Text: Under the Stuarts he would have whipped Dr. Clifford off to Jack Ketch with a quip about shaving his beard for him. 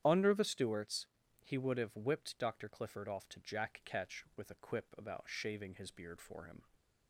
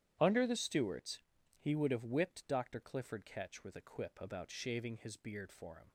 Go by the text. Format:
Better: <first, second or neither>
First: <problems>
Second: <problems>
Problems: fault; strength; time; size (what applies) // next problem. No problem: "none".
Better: first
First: starts louder than the rest; strong; until 1.0 s; 10 dB // pauses between "Stuarts" and "he"; at 1.0 s; 0.38 s long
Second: starts louder than the rest; strong; until 1.2 s; 11 dB // pauses between "Stuarts" and "he"; at 1.1 s; 0.38 s long // skips "off to Jack"; at 3.2 s